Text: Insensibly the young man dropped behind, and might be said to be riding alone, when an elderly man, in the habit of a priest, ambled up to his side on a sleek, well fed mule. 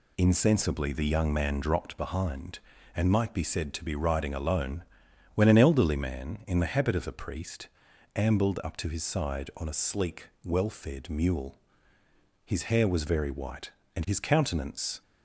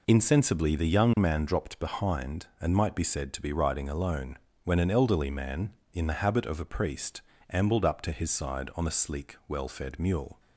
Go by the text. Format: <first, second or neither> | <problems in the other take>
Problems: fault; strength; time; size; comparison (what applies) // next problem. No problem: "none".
second | goes on to say "His hair was very white and his countenance"; strong; from 12.4 s on; 2.5 s long